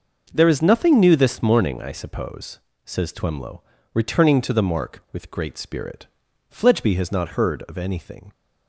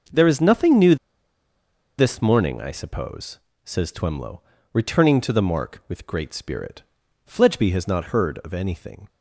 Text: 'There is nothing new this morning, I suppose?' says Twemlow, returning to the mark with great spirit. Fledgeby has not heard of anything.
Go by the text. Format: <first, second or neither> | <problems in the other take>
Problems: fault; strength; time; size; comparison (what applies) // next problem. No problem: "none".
first | starts louder than the rest; noticeable; until 2.1 s; 6 dB; noticeable in the first // pauses between "new" and "this"; at 0.9 s; 1.0 s long